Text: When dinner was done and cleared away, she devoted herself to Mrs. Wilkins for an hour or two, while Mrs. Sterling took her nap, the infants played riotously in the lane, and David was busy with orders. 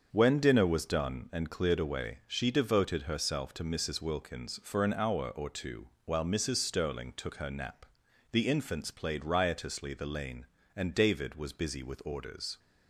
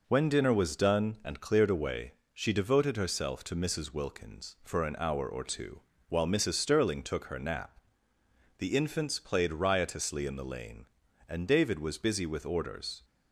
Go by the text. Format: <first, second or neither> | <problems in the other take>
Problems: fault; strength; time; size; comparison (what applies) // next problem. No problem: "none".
second | starts louder than the rest; until 1.1 s; 6.5 dB // skips "in"; at 9.9 s